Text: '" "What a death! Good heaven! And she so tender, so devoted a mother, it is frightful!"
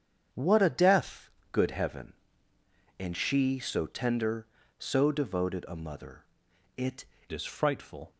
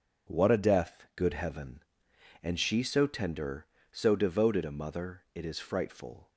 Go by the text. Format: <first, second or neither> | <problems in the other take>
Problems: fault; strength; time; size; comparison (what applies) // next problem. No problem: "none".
second | starts louder than the rest; strong; until 1.5 s; 7.5 dB // changes voice at "is"; from 7.3 s on; 0.8 s long